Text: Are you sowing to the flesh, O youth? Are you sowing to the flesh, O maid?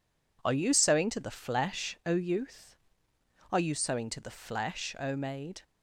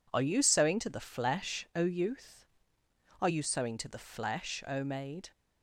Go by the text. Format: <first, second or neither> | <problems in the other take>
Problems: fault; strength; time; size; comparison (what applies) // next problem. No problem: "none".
neither | none